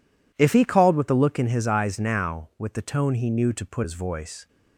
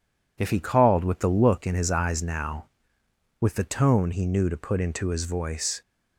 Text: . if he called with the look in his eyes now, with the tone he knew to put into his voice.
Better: second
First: skips "into"; at 3.8 s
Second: none

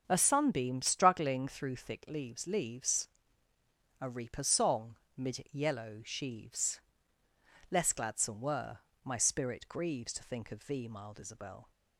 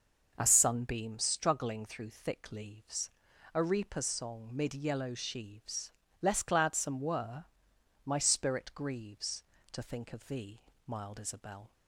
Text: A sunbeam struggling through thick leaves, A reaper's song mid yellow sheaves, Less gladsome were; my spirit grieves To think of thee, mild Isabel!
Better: second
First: starts louder than the rest; until 1.0 s; 6.5 dB // says "leaves" twice; at 2.4 s // pauses between "song" and "mid"; slight; at 4.9 s; 0.20 s long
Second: none

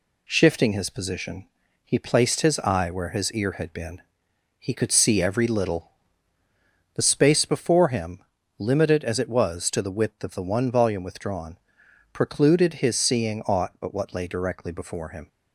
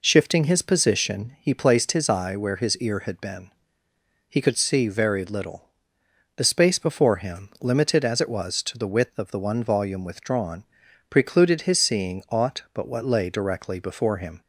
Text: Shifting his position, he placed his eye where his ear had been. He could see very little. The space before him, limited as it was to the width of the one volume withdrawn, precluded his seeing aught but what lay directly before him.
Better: second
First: says "every" for "very"; at 5.2 s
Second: none

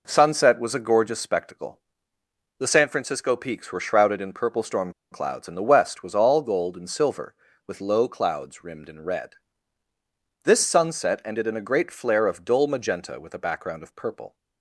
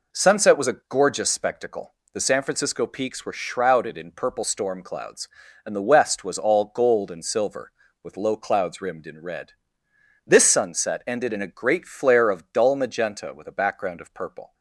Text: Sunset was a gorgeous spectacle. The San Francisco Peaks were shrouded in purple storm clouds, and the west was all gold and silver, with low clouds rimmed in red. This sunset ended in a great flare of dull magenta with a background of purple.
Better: second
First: pauses between "storm" and "clouds"; slight; at 4.9 s; 0.19 s long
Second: none

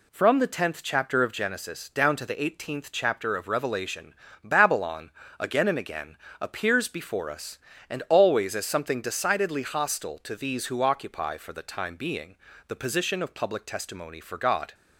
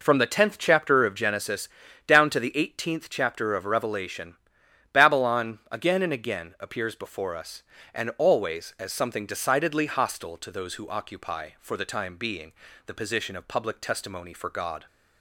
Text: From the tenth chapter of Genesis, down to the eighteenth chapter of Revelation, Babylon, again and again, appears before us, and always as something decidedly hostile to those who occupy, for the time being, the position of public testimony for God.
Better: second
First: says "these" for "those"; at 10.3 s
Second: none

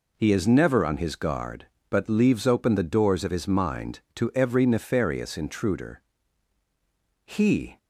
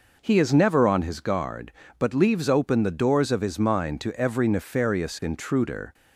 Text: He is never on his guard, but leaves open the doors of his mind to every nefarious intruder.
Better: second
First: goes on to say "He"; from 7.2 s on; 0.52 s long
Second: none

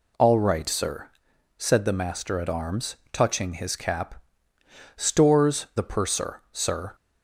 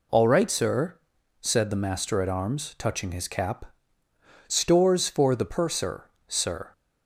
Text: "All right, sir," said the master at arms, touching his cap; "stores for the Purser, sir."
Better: second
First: skips "for"; at 5.7 s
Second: none

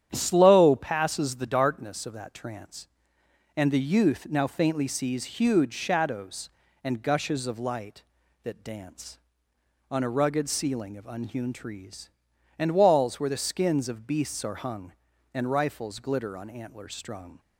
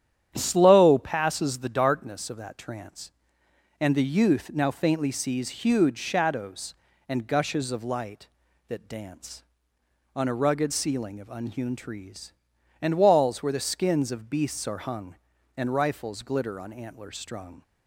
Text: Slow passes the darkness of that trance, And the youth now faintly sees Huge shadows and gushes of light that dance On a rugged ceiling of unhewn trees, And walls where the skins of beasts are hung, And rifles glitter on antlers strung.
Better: neither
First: starts louder than the rest; strong; until 1.1 s; 9.5 dB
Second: starts louder than the rest; strong; until 1.3 s; 9.5 dB

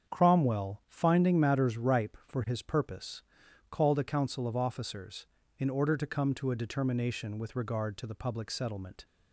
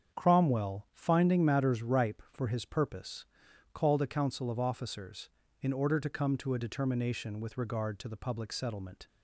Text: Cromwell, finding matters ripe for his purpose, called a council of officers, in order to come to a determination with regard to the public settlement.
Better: neither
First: starts louder than the rest; strong; until 1.1 s; 7.5 dB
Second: starts louder than the rest; strong; until 1.2 s; 7.5 dB

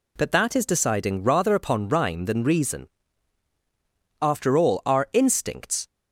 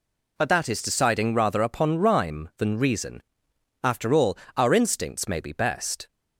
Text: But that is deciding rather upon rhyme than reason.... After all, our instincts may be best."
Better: second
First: stops before "may be best"; at 5.8 s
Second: none

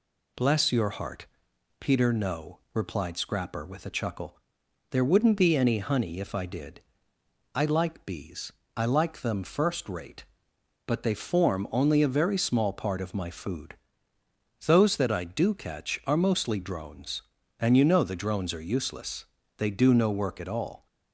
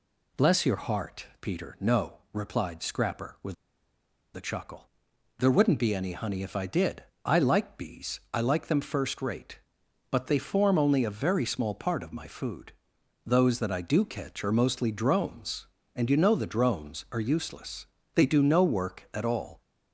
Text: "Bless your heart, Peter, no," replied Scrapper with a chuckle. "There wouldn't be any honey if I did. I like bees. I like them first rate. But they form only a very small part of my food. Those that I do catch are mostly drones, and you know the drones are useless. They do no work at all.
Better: first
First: none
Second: pauses between "with" and "a"; noticeable; at 3.5 s; 0.80 s long

